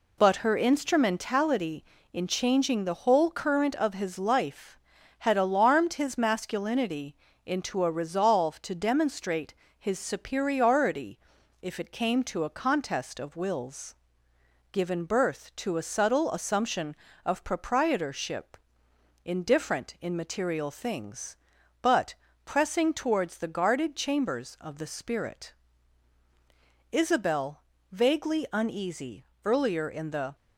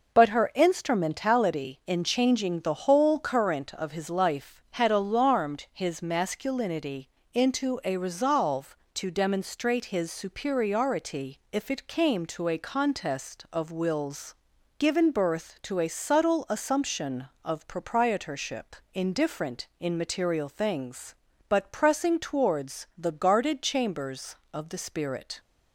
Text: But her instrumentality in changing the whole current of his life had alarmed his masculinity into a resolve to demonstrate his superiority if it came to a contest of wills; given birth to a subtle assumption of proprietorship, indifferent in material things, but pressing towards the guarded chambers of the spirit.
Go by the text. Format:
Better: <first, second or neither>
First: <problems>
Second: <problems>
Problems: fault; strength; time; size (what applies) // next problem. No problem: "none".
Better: second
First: pauses between "masculinity" and "into"; slight; at 7.1 s; 0.30 s long // pauses between "demonstrate" and "his"; slight; at 9.5 s; 0.26 s long // pauses between "superiority" and "if"; at 11.1 s; 0.42 s long // pauses between "but" and "pressing"; slight; at 22.1 s; 0.28 s long // goes on to say "Isabel vaguely uneasy earlier in the"; strong; from 26.9 s on; 3.4 s long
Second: pauses between "masculinity" and "into"; slight; at 7.0 s; 0.24 s long